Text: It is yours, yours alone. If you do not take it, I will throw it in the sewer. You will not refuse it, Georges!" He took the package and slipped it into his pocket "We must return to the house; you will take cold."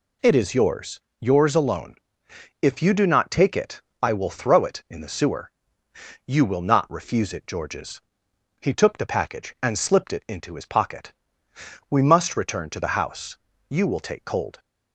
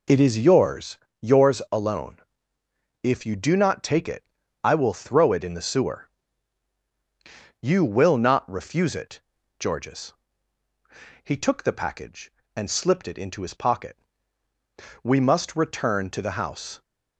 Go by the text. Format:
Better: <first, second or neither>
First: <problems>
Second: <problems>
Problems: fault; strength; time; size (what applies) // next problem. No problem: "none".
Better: first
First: pauses between "pocket" and "We"; noticeable; at 11.1 s; 0.76 s long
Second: pauses between "pocket" and "We"; at 13.9 s; 1.0 s long // stops before "you will take cold"; at 16.8 s